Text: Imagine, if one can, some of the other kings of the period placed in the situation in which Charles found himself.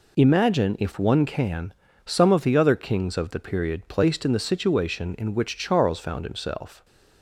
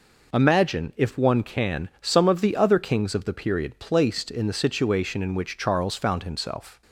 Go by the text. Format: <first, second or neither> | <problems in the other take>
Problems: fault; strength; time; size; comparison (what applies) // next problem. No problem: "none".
neither | none